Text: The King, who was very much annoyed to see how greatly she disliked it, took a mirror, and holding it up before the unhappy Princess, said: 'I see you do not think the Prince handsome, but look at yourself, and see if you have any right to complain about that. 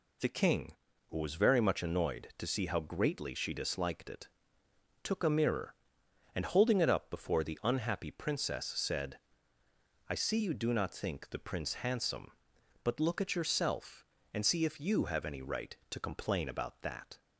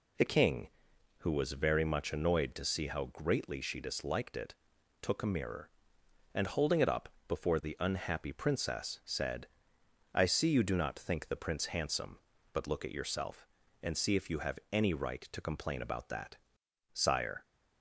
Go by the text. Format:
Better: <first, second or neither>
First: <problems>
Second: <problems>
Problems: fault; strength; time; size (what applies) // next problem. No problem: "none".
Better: first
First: none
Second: pauses between "up" and "before"; slight; at 7.0 s; 0.18 s long // goes on to say "Sire"; from 16.9 s on; 0.52 s long